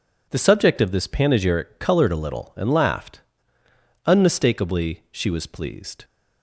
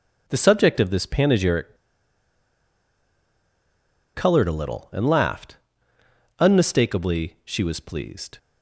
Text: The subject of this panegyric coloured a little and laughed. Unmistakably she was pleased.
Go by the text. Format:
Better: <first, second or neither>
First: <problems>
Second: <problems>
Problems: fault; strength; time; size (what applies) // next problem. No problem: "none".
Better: first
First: none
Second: pauses between "panegyric" and "coloured"; strong; at 1.7 s; 2.3 s long